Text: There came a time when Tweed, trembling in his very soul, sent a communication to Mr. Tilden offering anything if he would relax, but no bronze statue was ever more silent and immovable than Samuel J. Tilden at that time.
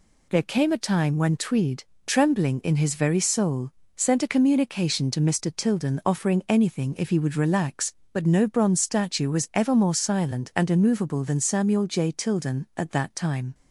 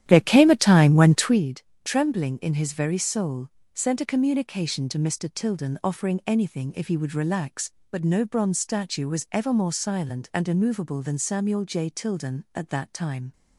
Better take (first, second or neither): first